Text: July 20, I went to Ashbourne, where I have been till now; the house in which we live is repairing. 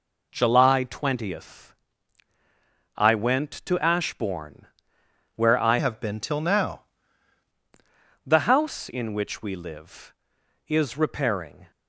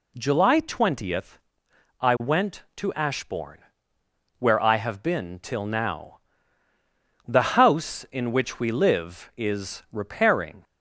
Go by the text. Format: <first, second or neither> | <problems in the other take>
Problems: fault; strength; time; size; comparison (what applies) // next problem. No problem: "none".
second | changes voice from "have" to "now"; from 5.7 to 6.8 s; 1.1 s long